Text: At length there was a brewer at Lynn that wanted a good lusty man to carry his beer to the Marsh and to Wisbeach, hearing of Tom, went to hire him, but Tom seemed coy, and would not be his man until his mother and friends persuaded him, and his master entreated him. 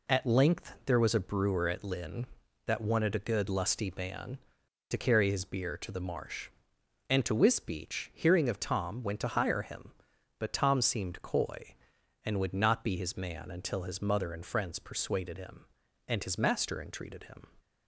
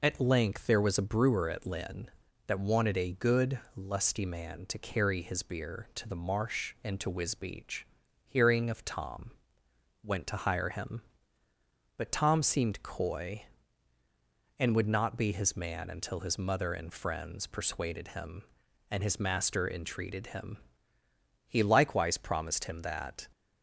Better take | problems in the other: first | pauses between "good" and "lusty"; slight; at 3.5 s; 0.16 s long // goes on to say "He likewise promised him that"; strong; from 21.4 s on; 1.8 s long

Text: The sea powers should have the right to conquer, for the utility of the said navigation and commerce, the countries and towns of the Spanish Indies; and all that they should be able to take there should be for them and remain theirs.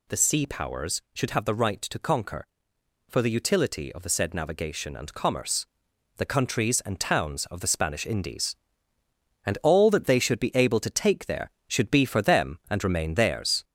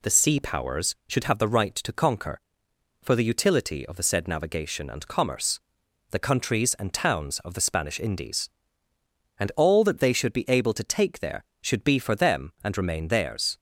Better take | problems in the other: second | gets louder; slight; throughout; 3 dB

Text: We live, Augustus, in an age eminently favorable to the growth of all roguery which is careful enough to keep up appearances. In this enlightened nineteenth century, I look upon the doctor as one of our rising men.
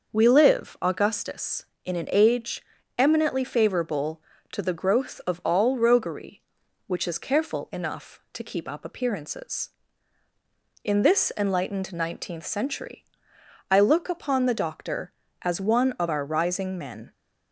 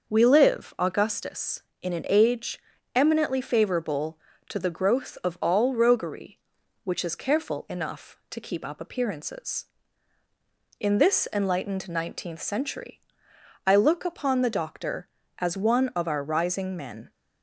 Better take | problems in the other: neither | starts louder than the rest; the same in both // pauses between "age" and "eminently"; slight; the same in both

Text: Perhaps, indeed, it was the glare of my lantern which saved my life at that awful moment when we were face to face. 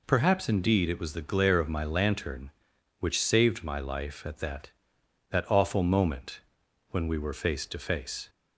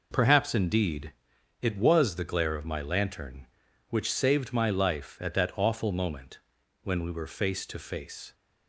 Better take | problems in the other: second | says "that" twice; at 5.2 s // pauses between "moment" and "when"; noticeable; at 6.4 s; 0.48 s long; also in the second

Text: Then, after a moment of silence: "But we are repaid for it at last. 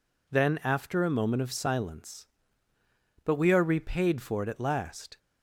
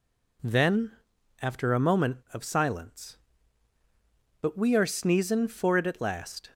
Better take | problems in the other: first | says "sneezin" for "repaid"; at 4.8 s

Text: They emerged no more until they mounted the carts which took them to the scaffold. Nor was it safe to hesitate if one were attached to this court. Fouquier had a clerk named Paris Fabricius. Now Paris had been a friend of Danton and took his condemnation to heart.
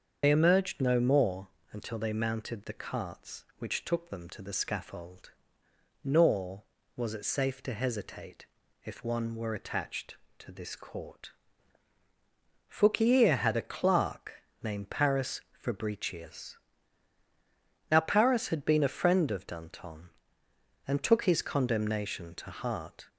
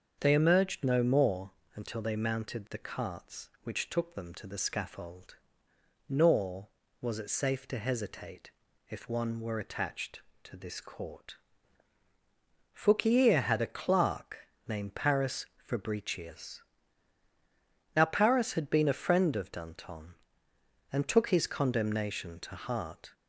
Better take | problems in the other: second | loses the start of "They"; at 0.2 s; 70 ms // starts louder than the rest; until 1.2 s; 7 dB; also in the second // pauses between "more" and "until"; slight; at 1.4 s; 0.24 s long; slight in the second // pauses between "hesitate" and "if"; at 8.4 s; 0.38 s long; also in the second // pauses between "clerk" and "named"; slight; at 14.3 s; 0.28 s long; slight in the second

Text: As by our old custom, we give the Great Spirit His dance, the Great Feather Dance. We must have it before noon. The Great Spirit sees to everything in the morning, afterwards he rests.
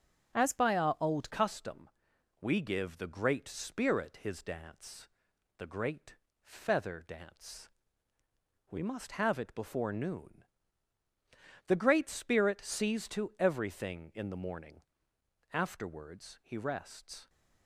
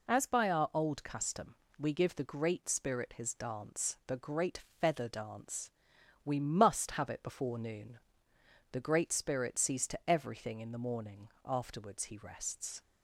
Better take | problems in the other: second | starts louder than the rest; noticeable; until 1.4 s; 6 dB // changes voice at "custom"; from 1.2 s on; 16.0 s long // pauses between "Great" and "Feather"; slight; at 6.1 s; 0.26 s long; slight in the second

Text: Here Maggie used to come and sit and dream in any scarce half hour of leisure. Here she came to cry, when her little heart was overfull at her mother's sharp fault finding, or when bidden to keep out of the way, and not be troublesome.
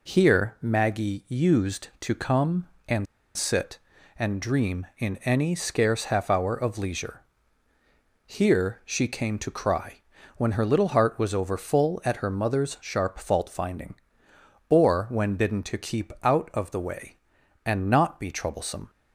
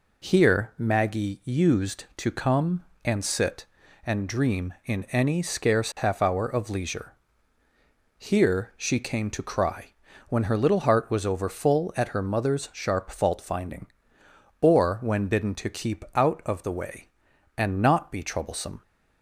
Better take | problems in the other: second | pauses between "and" and "sit"; slight; at 3.0 s; 0.31 s long

